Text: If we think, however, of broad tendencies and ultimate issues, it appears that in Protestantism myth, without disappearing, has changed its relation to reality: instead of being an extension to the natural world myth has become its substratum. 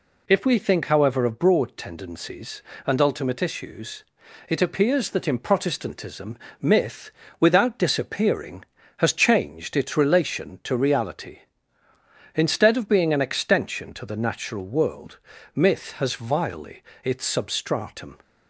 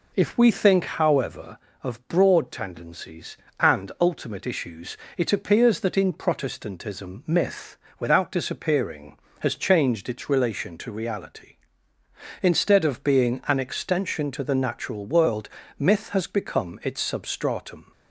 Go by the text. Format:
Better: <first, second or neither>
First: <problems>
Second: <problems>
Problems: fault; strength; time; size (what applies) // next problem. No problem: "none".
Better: second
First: pauses between "Protestantism" and "myth"; slight; at 6.3 s; 0.22 s long // pauses between "world" and "myth"; slight; at 15.1 s; 0.34 s long // says "vilely" for "become"; at 16.1 s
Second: pauses between "world" and "myth"; slight; at 15.4 s; 0.30 s long